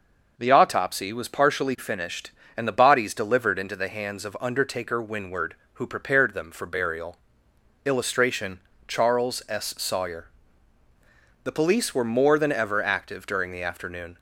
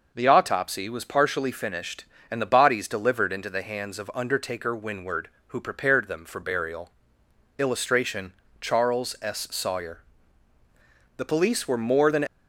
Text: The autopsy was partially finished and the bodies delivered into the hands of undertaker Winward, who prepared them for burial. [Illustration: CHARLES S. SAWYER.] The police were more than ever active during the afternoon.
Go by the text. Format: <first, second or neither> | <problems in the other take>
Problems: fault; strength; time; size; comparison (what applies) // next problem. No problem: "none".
first | stops before "ever active during the afternoon"; at 12.2 s